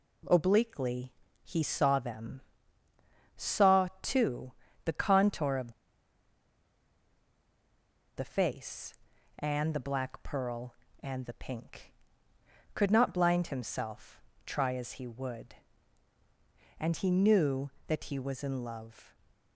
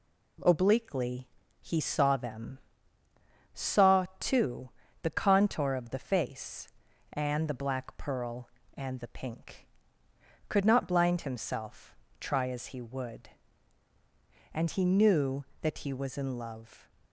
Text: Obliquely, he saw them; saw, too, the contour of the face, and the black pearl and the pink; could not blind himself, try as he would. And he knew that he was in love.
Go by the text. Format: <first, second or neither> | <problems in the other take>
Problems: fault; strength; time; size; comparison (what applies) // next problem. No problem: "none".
second | pauses between "of" and "the"; strong; at 5.7 s; 2.4 s long